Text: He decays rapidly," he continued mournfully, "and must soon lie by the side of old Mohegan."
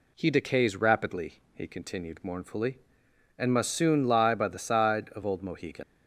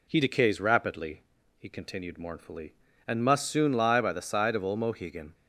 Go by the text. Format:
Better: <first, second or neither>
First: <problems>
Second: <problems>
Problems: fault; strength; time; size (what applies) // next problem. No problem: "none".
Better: second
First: leaves "Mohegan" unfinished; at 5.8 s; 110 ms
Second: none